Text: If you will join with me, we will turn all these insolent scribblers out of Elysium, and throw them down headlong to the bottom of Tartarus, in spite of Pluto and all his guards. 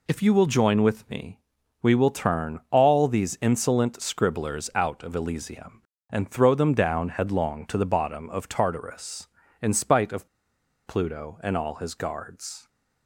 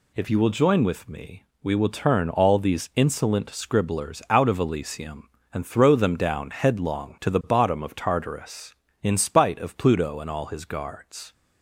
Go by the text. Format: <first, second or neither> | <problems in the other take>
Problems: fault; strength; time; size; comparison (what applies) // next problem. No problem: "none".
second | pauses between "of" and "Pluto"; noticeable; at 10.2 s; 0.59 s long